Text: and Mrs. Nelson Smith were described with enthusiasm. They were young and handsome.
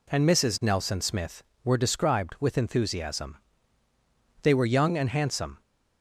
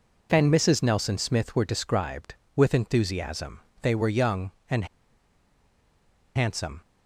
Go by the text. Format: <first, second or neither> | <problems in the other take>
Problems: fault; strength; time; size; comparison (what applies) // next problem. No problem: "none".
first | pauses between "and" and "handsome"; strong; at 4.8 s; 1.5 s long